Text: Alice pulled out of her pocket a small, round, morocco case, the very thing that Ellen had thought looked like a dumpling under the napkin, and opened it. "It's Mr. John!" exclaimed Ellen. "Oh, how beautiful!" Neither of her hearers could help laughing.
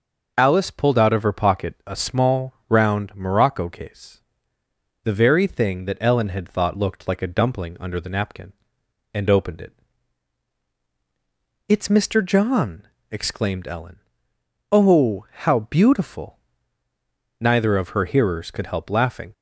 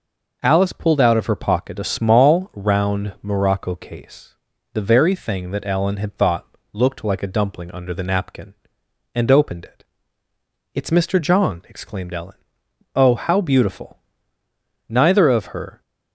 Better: first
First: none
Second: pauses between "thought" and "looked"; slight; at 6.4 s; 0.26 s long // stops before "hearers could help laughing"; at 15.8 s

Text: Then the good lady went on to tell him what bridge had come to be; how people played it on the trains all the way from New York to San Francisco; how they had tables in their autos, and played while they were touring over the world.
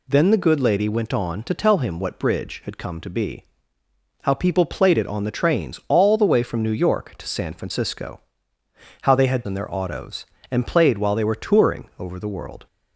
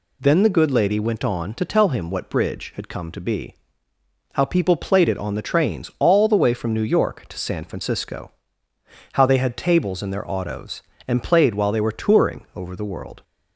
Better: second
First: skips "tables"; at 9.4 s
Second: none

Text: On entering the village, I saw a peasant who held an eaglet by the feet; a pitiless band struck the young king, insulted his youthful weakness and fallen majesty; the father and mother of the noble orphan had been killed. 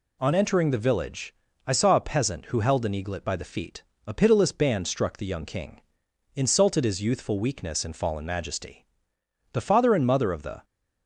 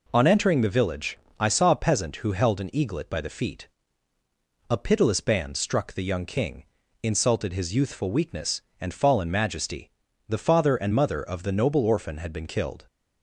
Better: second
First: stops before "noble orphan had been killed"; at 10.6 s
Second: none

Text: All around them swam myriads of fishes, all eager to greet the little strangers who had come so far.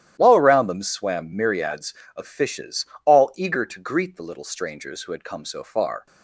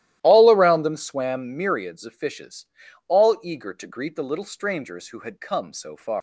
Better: first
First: starts louder than the rest; strong; until 1.2 s; 12.5 dB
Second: starts louder than the rest; strong; until 1.2 s; 14 dB // leaves "far" unfinished; at 6.1 s; 185 ms

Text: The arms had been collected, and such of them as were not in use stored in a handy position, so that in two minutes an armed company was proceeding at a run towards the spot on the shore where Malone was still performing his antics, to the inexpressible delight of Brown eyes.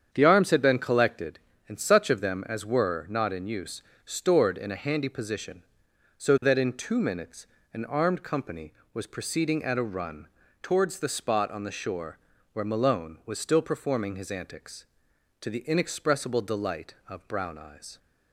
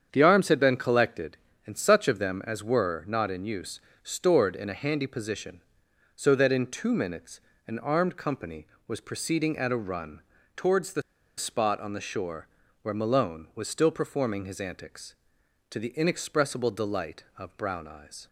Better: first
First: starts louder than the rest; strong; until 1.1 s; 7.5 dB // pauses between "use" and "stored"; slight; at 3.8 s; 0.22 s long // pauses between "minutes" and "an"; slight; at 7.4 s; 0.28 s long // pauses between "run" and "towards"; slight; at 10.2 s; 0.34 s long // pauses between "shore" and "where"; slight; at 12.1 s; 0.36 s long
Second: starts louder than the rest; strong; until 1.1 s; 7.5 dB // pauses between "use" and "stored"; slight; at 3.7 s; 0.22 s long // pauses between "minutes" and "an"; slight; at 7.3 s; 0.28 s long // pauses between "run" and "towards"; slight; at 10.2 s; 0.34 s long // pauses between "the" and "spot"; slight; at 11.0 s; 0.35 s long // pauses between "shore" and "where"; slight; at 12.4 s; 0.36 s long

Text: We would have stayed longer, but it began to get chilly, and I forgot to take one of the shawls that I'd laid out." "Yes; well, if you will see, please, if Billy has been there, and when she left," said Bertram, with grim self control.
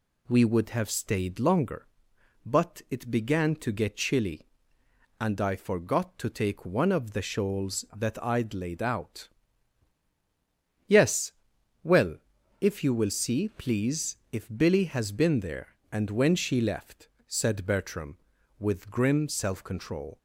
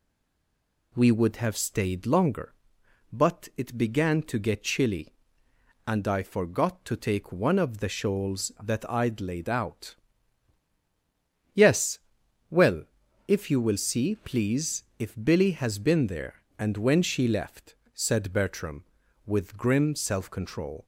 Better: first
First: none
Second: stays silent before the first word; slight; until 0.9 s; 0.9 s long

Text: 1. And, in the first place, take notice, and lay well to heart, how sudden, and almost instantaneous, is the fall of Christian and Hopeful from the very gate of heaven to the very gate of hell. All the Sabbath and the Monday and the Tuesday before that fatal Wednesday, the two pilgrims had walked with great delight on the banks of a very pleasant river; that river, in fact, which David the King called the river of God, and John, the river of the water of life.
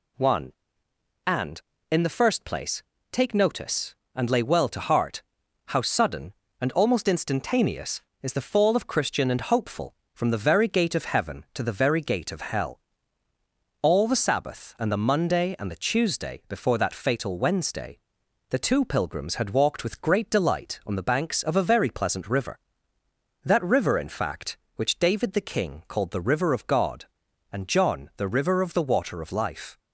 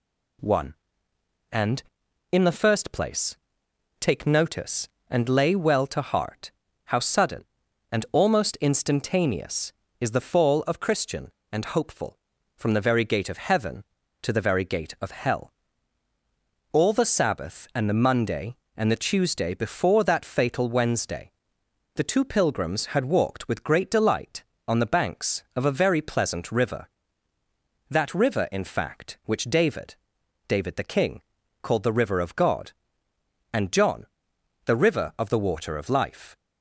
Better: first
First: none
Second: says "David" twice; at 30.4 s // pauses between "King" and "called"; at 31.2 s; 0.40 s long

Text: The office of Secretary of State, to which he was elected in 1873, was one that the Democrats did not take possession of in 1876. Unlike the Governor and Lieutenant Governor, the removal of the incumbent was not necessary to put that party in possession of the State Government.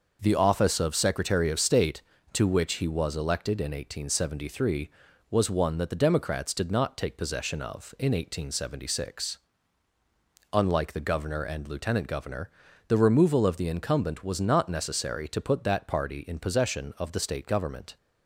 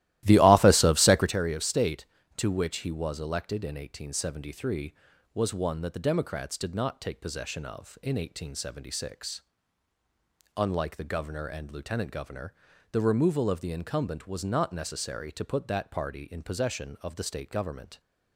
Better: first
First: none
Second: starts louder than the rest; strong; until 1.4 s; 15.5 dB

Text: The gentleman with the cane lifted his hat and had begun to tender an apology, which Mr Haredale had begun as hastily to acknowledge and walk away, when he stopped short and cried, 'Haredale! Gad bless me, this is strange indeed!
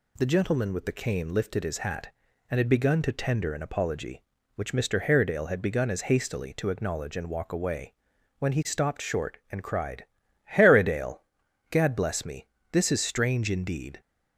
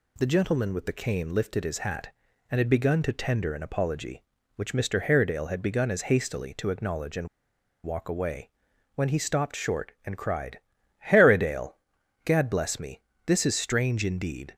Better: first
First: none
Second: pauses between "and" and "walk"; noticeable; at 7.2 s; 0.56 s long

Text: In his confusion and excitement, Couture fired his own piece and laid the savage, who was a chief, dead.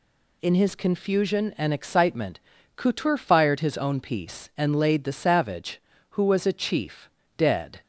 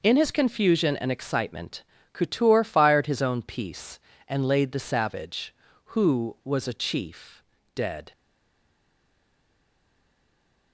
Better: first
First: none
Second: stays silent after the last word; strong; from 8.1 s on; 2.6 s long

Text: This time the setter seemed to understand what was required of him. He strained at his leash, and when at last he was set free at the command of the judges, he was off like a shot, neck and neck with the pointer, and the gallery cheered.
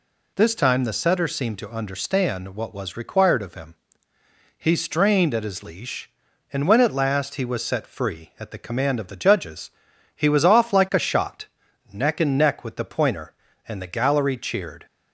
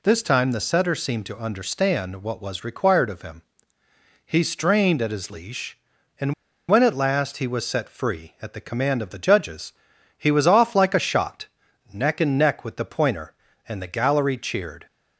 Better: first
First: none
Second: pauses between "and" and "when"; slight; at 6.3 s; 0.35 s long

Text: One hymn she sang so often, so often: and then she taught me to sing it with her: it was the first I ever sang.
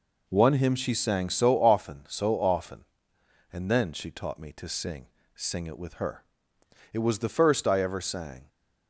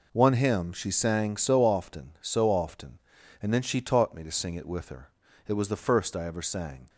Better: second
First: says "sing" twice; at 5.3 s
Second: none

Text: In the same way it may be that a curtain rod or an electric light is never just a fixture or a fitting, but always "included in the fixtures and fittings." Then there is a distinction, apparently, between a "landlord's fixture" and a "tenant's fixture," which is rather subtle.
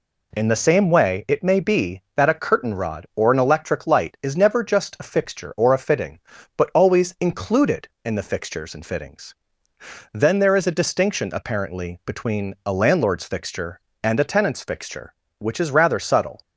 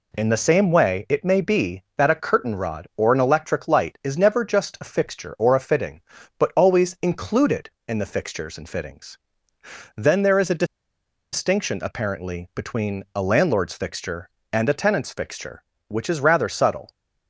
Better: first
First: none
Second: pauses between "a" and "distinction"; noticeable; at 10.6 s; 0.68 s long

